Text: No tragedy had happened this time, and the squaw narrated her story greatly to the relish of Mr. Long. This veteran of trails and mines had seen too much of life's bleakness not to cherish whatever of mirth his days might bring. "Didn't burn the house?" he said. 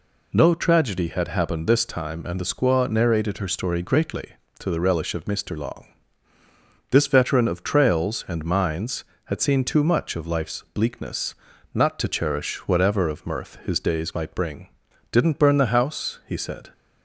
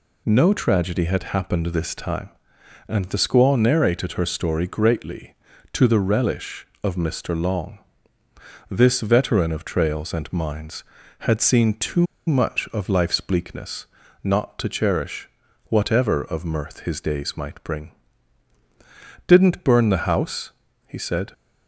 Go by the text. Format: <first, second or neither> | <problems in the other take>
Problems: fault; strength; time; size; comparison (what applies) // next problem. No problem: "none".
first | pauses between "too" and "much"; slight; at 12.0 s; 0.21 s long // pauses between "bleakness" and "not"; at 13.8 s; 0.38 s long; also in the first // pauses between "cherish" and "whatever"; slight; at 15.2 s; 0.36 s long